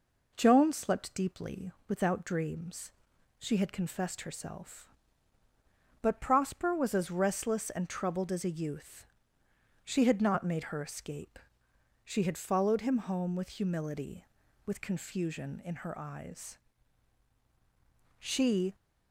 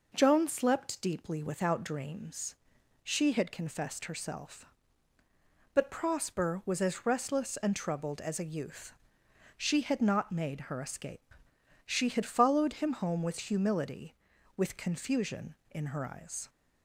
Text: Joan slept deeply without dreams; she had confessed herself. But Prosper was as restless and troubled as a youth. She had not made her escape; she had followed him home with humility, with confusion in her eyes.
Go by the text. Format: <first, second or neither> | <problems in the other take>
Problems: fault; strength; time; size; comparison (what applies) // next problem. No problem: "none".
second | pauses between "deeply" and "without"; slight; at 1.7 s; 0.16 s long // goes on to say "She"; from 18.1 s on; 0.58 s long